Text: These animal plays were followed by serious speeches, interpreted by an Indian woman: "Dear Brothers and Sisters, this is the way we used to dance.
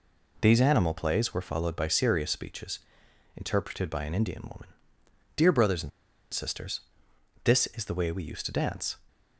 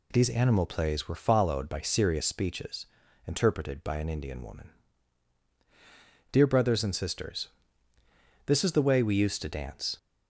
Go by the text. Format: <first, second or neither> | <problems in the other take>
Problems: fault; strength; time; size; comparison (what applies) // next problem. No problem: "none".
second | pauses between "and" and "Sisters"; at 5.9 s; 0.42 s long